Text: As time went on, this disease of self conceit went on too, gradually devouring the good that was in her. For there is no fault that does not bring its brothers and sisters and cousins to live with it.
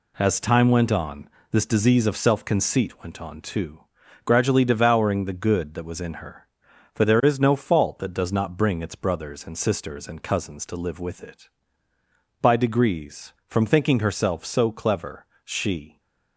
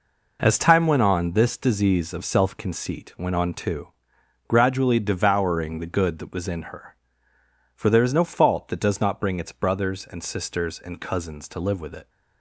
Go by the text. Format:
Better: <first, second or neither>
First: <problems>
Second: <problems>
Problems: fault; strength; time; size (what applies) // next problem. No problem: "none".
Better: second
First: goes on to say "By degrees from thinking herself so clever she"; strong; from 12.4 s on; 3.5 s long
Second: none